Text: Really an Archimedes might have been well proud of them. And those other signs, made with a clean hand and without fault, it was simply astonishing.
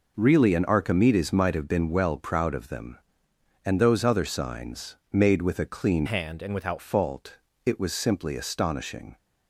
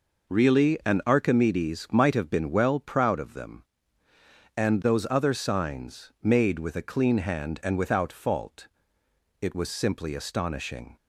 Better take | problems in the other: second | changes voice from "hand" to "without"; from 6.0 to 6.7 s; 0.7 s long

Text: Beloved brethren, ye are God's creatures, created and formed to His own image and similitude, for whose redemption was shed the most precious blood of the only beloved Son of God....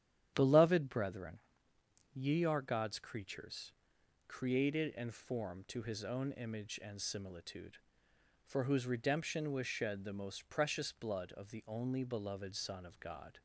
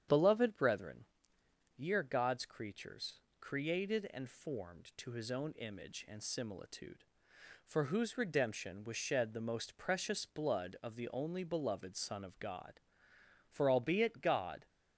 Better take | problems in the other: first | starts louder than the rest; strong; until 1.8 s; 9 dB; strong in the first // goes on to say "For albeit God"; noticeable; from 13.5 s on; 1.1 s long

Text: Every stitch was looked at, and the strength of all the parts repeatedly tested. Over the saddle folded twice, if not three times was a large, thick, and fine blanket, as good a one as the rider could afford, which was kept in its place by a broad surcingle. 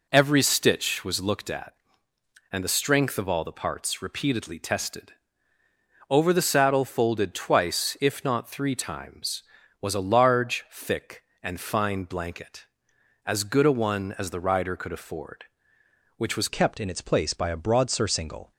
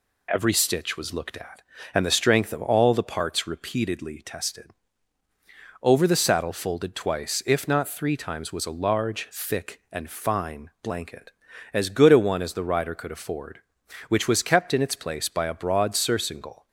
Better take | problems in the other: second | changes voice at "kept"; from 16.4 s on; 2.1 s long

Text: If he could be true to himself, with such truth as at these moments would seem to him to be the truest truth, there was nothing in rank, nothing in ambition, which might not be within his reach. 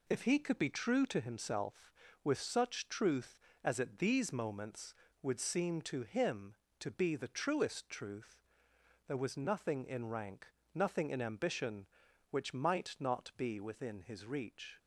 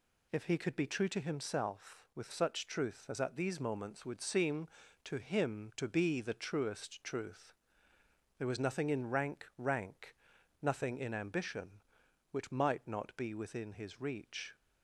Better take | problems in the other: first | says "rank" twice; at 9.5 s

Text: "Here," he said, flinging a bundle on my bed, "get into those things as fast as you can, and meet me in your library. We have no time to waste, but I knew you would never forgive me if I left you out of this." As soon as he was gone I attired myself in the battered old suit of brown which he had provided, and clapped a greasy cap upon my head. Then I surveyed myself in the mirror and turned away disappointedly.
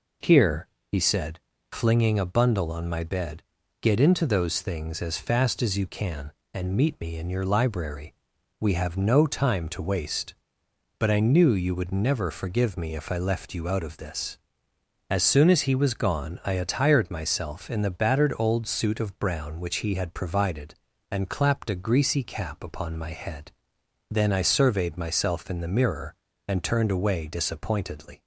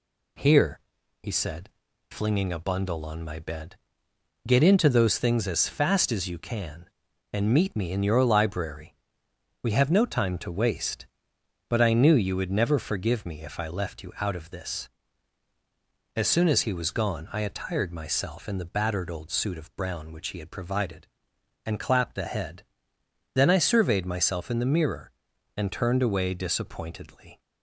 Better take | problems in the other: first | skips "greasy cap upon my"; at 22.2 s

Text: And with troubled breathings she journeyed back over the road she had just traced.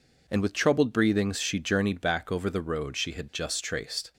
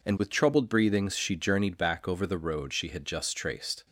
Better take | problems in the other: neither | none

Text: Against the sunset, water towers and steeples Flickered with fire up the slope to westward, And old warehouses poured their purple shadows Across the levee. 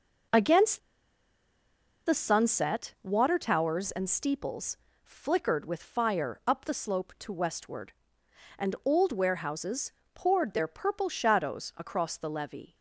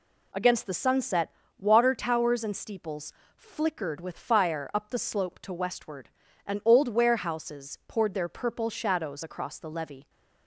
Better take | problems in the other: second | pauses between "Against" and "the"; strong; at 0.7 s; 1.2 s long // pauses between "steeples" and "Flickered"; slight; at 4.7 s; 0.28 s long; slight in the second // pauses between "warehouses" and "poured"; slight; at 9.9 s; 0.22 s long

